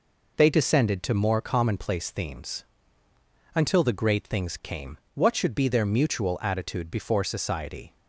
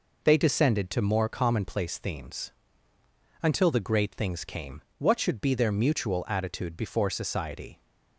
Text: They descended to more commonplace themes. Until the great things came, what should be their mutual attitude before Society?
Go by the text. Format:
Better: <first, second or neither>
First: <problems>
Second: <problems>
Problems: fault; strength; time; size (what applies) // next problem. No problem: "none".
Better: neither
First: none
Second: none